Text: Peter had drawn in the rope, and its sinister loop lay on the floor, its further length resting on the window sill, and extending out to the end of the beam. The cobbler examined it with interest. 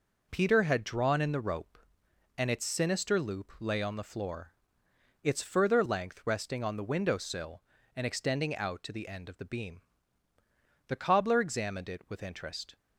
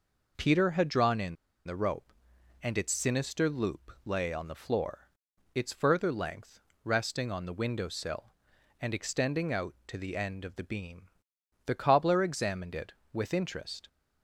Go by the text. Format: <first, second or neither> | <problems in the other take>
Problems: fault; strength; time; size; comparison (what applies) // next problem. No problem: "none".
first | pauses between "in" and "the"; slight; at 1.3 s; 0.30 s long // pauses between "length" and "resting"; slight; at 6.5 s; 0.24 s long